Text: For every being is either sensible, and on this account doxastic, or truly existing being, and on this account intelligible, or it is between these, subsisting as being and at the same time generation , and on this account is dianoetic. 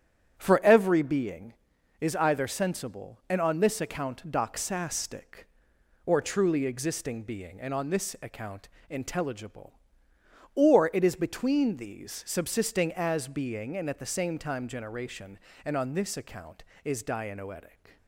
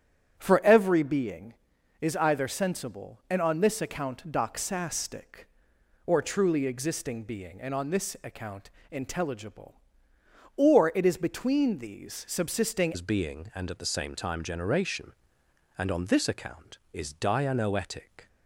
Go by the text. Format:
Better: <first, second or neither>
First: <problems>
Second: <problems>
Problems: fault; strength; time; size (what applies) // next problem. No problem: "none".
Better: first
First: starts louder than the rest; strong; until 1.3 s; 9 dB // pauses between "account" and "intelligible"; slight; at 8.6 s; 0.20 s long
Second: starts louder than the rest; strong; until 1.3 s; 9.5 dB // pauses between "account" and "intelligible"; slight; at 8.7 s; 0.20 s long // changes voice at "as"; from 12.9 s on; 5.3 s long